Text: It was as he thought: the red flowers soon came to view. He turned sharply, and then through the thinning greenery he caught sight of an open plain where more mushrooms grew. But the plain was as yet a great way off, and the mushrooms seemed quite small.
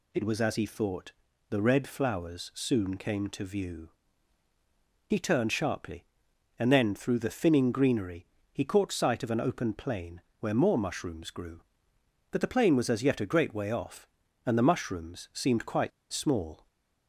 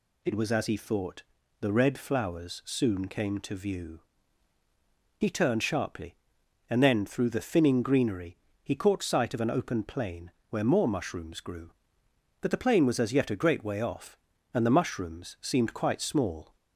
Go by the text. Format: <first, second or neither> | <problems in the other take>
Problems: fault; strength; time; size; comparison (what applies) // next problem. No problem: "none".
second | pauses between "greenery" and "he"; slight; at 8.2 s; 0.26 s long; slight in the second // pauses between "plain" and "where"; slight; at 10.2 s; 0.18 s long; slight in the second // pauses between "quite" and "small"; slight; at 15.9 s; 0.22 s long